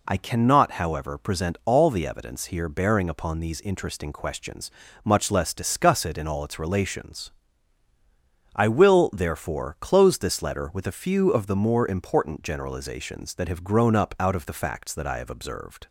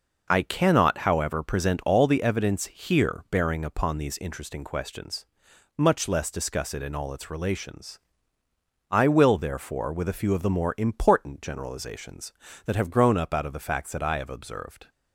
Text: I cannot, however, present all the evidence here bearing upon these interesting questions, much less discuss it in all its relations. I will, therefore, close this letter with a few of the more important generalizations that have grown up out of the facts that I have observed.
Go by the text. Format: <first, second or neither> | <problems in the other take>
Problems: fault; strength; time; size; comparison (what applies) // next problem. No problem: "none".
first | skips "close this letter"; at 9.9 s